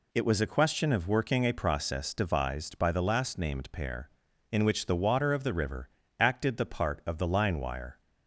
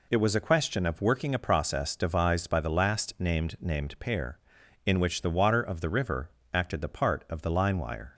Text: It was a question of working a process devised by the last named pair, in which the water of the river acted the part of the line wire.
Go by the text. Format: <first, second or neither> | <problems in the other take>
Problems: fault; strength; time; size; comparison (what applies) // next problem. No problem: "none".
first | says "named" twice; at 3.5 s // pauses between "river" and "acted"; slight; at 6.2 s; 0.24 s long; slight in the first